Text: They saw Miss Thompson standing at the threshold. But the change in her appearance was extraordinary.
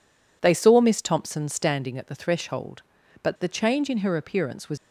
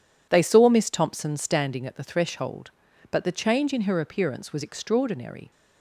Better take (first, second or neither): second